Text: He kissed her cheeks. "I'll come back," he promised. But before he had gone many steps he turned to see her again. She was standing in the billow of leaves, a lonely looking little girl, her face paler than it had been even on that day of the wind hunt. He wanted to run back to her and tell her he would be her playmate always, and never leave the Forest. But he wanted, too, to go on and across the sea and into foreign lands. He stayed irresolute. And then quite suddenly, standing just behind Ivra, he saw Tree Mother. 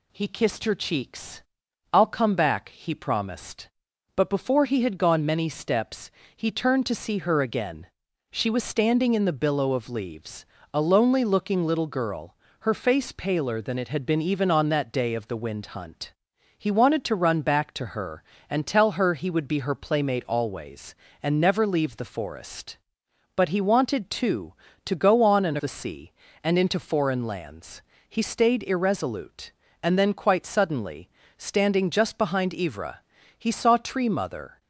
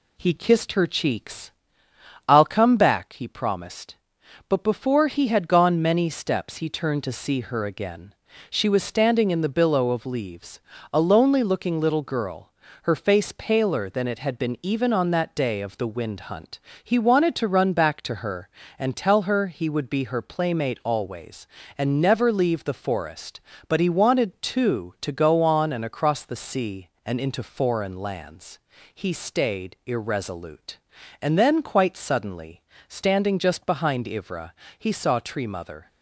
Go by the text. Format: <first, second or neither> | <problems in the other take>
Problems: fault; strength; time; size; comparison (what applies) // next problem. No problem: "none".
second | pauses between "steps" and "he"; slight; at 6.1 s; 0.24 s long // skips "across"; at 25.5 s